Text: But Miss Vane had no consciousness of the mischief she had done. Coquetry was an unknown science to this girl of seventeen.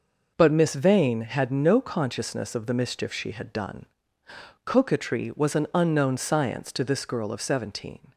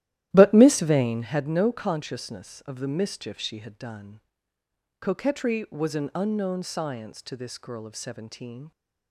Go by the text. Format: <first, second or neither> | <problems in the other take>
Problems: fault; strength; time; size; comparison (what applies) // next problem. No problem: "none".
first | starts louder than the rest; strong; until 1.5 s; 13.5 dB